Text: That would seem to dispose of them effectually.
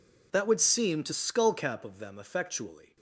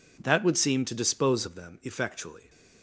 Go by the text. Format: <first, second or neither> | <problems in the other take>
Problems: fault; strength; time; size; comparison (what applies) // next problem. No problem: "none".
second | says "skullcap" for "dispose"; at 1.1 s